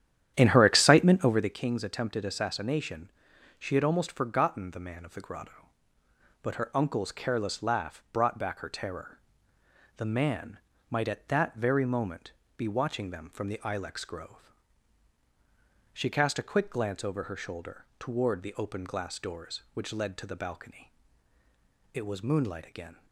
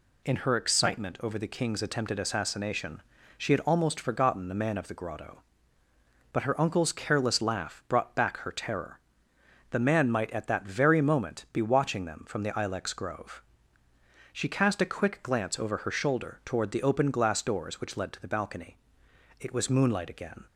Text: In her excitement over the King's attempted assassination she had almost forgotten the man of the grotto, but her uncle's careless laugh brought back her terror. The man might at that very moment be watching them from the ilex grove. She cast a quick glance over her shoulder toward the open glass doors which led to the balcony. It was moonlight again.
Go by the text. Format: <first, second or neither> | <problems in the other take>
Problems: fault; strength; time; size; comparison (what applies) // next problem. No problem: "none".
second | starts louder than the rest; strong; until 1.6 s; 10.5 dB // pauses between "assassination" and "she"; noticeable; at 3.0 s; 0.50 s long; slight in the second // pauses between "man" and "might"; slight; at 10.5 s; 0.32 s long // pauses between "moment" and "be"; slight; at 12.3 s; 0.24 s long